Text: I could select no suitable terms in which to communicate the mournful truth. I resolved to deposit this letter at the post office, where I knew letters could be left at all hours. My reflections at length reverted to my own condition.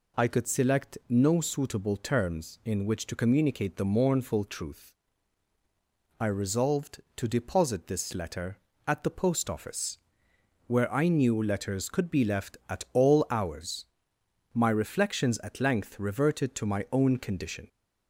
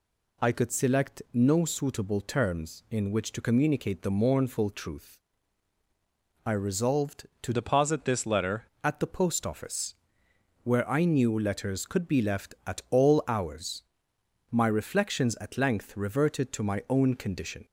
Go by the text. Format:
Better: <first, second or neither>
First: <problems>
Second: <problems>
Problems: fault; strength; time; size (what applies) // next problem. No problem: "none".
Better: first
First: none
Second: changes voice from "deposit" to "letter"; from 7.5 to 8.6 s; 1.1 s long